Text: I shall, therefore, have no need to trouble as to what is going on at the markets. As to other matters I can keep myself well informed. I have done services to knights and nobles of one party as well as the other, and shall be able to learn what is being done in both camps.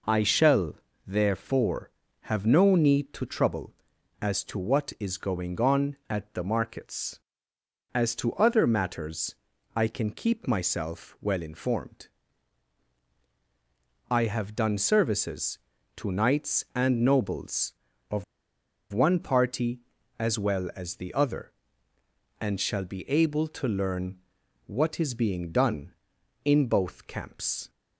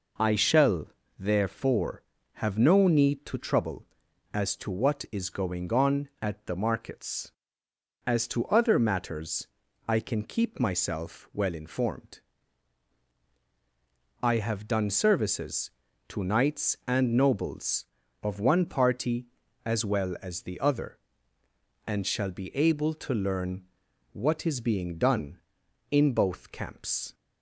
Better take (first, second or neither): second